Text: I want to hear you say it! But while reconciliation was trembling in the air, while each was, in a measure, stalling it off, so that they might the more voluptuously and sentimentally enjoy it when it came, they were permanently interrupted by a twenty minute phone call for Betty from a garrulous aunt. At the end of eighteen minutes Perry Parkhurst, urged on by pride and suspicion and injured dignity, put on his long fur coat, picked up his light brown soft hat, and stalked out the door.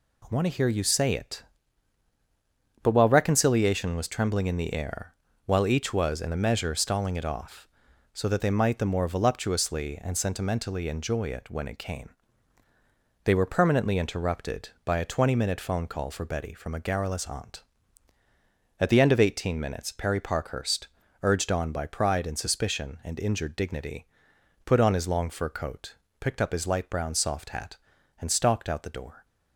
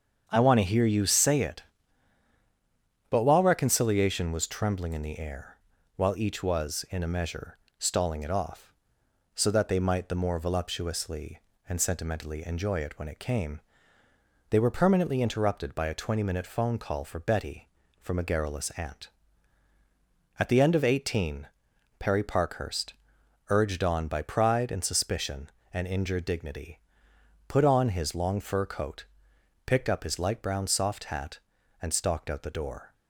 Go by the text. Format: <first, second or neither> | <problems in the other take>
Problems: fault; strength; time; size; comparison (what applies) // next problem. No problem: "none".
first | starts louder than the rest; strong; until 1.2 s; 7 dB // skips "minutes"; at 21.7 s